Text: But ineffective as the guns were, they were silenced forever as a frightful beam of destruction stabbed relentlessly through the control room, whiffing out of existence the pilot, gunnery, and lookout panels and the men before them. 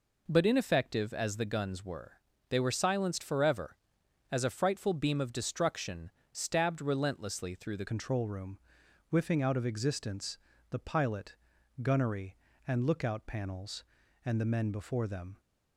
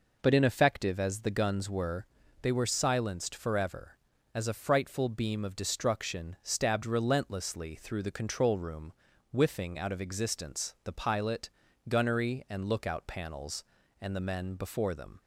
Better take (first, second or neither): second